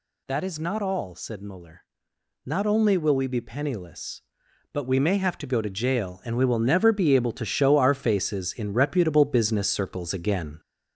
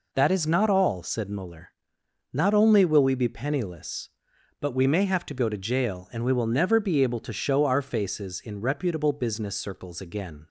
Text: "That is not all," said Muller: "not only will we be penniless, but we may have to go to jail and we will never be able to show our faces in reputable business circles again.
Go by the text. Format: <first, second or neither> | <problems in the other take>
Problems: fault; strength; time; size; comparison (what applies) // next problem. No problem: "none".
second | gets louder; throughout; 3.5 dB